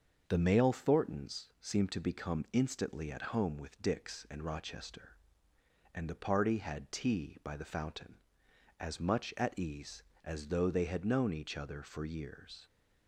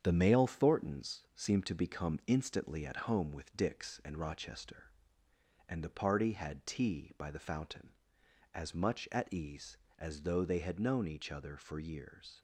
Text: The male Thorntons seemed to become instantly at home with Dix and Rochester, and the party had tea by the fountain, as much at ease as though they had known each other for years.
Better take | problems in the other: first | gets quieter; noticeable; throughout; 5.5 dB // starts louder than the rest; strong; until 1.0 s; 8 dB; also in the first

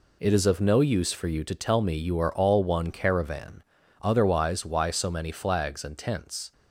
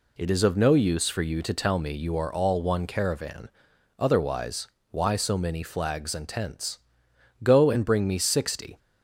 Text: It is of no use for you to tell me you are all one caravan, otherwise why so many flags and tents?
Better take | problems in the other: first | pauses between "otherwise" and "why"; slight; at 4.6 s; 0.22 s long // goes on to say "Go and bring me sixty"; from 7.4 s on; 1.3 s long

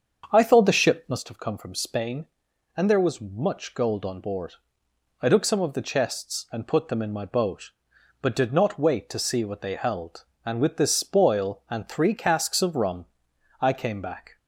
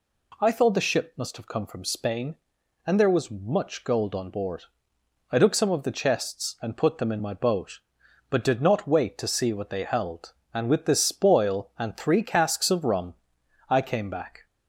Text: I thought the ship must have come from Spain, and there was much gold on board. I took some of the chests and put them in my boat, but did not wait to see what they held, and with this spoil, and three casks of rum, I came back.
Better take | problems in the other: second | starts louder than the rest; until 1.2 s; 7 dB

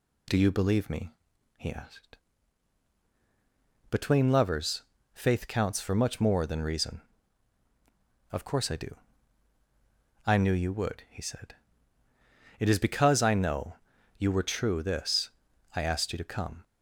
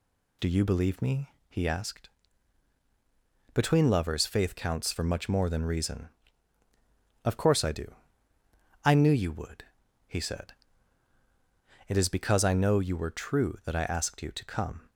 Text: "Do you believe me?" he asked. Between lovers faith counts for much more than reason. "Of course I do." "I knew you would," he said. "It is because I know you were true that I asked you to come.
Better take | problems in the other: second | pauses between "lovers" and "faith"; slight; at 4.8 s; 0.32 s long // pauses between "know" and "you"; at 13.7 s; 0.42 s long // says "this" for "that"; at 14.8 s

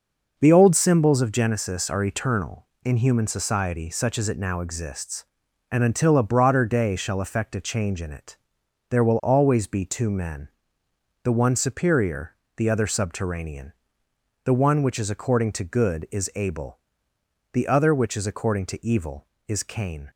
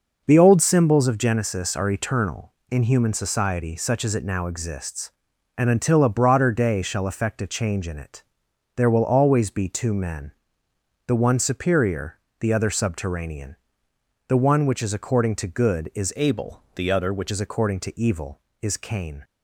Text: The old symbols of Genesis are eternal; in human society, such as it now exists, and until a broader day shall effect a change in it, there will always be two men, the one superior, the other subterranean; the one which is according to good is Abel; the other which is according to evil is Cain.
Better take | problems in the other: first | changes voice from "Abel" to "which"; from 16.1 to 17.3 s; 1.2 s long

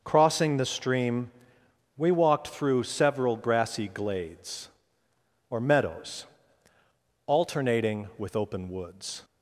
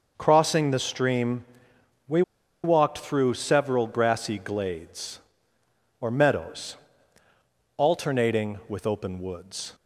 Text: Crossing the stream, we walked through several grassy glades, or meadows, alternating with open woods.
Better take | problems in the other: first | pauses between "we" and "walked"; at 2.2 s; 0.42 s long

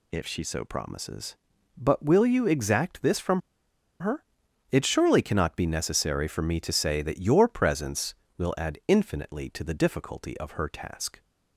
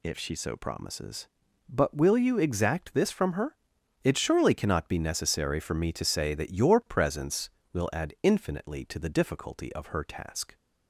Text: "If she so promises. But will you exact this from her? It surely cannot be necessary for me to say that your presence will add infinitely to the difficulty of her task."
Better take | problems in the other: second | pauses between "from" and "her"; noticeable; at 3.4 s; 0.59 s long

